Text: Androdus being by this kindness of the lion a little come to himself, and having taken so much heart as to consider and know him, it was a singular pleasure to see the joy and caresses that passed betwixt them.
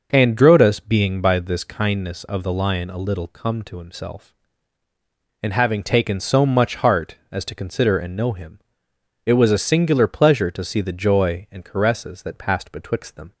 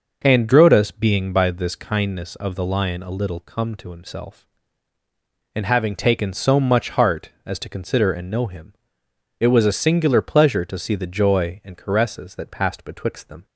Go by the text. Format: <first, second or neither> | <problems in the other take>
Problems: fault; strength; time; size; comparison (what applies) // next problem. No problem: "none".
neither | none